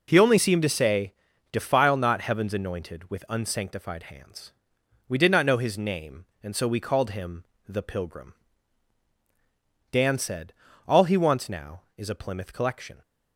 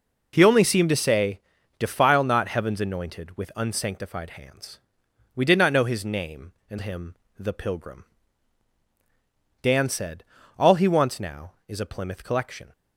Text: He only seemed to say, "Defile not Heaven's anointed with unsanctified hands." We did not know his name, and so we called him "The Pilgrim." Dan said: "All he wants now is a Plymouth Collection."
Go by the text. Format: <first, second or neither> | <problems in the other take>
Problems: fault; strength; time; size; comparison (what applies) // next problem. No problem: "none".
first | skips "so we called"; at 6.7 s // pauses between "him" and "The"; slight; at 7.1 s; 0.24 s long; slight in the first